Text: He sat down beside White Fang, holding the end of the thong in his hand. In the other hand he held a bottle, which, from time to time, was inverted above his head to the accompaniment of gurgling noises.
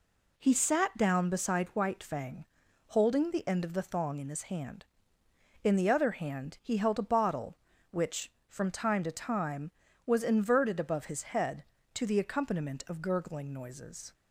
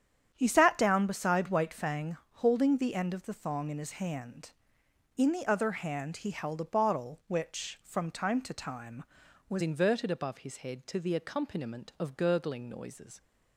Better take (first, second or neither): first